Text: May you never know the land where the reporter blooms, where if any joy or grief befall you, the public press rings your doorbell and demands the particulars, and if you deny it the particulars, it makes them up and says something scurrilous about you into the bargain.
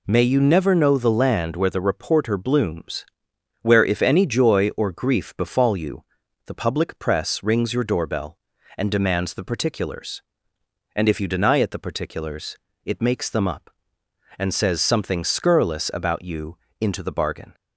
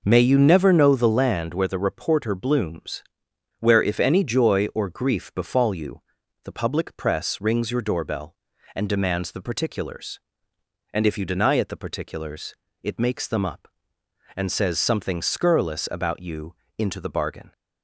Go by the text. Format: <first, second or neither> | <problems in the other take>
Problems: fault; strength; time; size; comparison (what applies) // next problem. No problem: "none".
first | starts louder than the rest; noticeable; until 1.3 s; 5 dB // pauses between "you" and "into"; slight; at 16.5 s; 0.22 s long; slight in the first